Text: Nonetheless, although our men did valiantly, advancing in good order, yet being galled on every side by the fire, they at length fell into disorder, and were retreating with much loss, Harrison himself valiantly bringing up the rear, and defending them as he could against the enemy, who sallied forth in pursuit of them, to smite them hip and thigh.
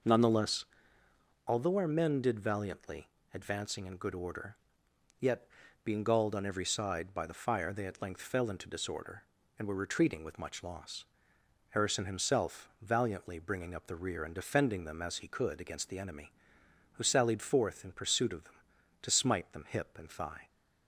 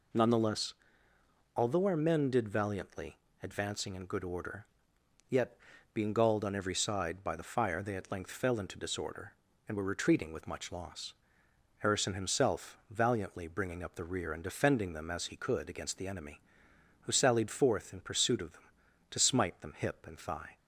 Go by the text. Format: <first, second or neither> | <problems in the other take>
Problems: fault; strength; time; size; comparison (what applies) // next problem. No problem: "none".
second | starts louder than the rest; noticeable; until 1.3 s; 5.5 dB // pauses between "yet" and "being"; at 5.4 s; 0.38 s long; also in the second